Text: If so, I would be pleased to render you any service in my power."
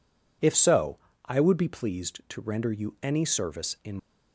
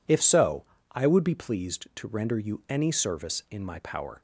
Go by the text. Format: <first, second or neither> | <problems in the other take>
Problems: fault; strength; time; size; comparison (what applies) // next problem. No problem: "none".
second | stops before "my power"; at 3.9 s